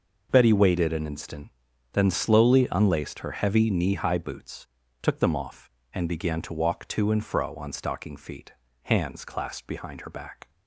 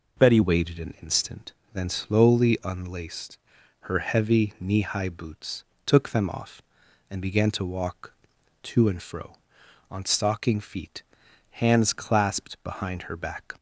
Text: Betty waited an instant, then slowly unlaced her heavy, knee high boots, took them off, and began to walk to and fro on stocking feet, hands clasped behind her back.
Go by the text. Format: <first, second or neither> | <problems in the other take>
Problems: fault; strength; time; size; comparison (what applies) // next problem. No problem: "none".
first | changes voice at "waited"; from 0.4 s on; 13.1 s long // pauses between "unlaced" and "her"; at 3.3 s; 0.44 s long